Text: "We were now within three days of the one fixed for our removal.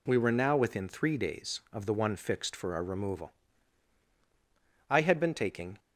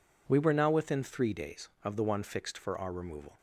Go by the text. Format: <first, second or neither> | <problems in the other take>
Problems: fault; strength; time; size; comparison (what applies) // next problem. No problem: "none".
second | goes on to say "I had been taking"; noticeable; from 4.8 s on; 0.90 s long